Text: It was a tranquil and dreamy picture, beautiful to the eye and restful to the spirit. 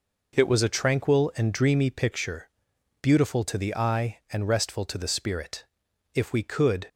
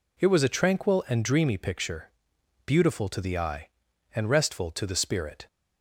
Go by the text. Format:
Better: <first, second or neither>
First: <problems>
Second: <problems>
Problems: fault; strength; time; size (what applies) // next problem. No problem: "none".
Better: second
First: goes on to say "If we could"; noticeable; from 6.1 s on; 0.74 s long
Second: none